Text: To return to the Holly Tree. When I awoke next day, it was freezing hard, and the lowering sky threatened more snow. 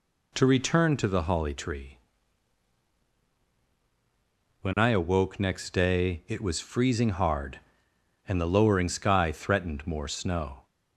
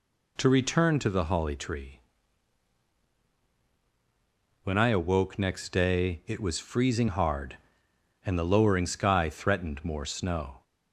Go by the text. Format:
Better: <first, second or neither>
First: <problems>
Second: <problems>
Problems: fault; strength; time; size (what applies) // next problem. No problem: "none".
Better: neither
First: none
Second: none